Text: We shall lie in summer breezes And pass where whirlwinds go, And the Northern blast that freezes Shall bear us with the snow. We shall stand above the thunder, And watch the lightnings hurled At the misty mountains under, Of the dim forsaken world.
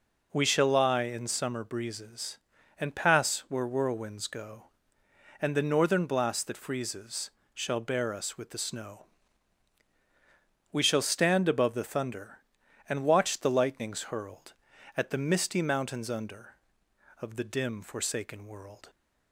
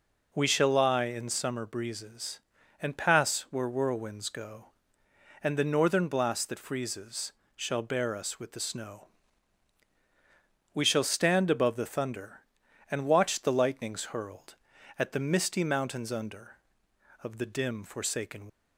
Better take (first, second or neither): first